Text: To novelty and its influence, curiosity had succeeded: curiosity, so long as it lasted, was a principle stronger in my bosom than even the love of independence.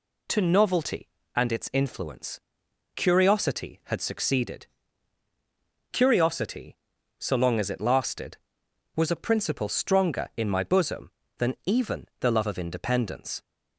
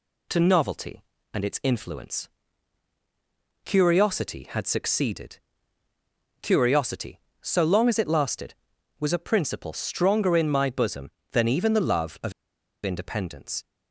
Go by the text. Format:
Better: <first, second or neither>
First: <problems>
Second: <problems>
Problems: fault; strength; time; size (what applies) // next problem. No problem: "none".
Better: first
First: none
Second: pauses between "of" and "independence"; noticeable; at 12.3 s; 0.53 s long